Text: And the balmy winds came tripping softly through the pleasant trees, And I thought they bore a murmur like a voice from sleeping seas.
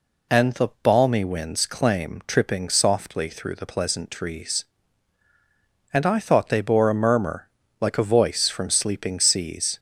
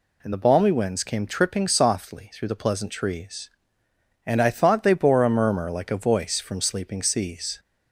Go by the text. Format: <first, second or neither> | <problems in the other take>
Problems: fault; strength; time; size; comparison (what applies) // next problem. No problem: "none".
second | says "claim" for "came"; at 1.6 s // pauses between "murmur" and "like"; slight; at 7.4 s; 0.32 s long